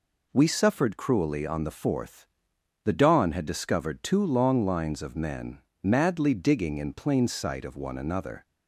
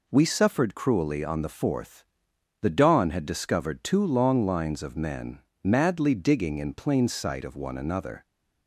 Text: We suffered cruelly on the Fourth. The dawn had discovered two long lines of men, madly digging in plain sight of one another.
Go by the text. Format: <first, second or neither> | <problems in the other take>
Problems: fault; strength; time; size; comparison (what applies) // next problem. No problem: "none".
neither | none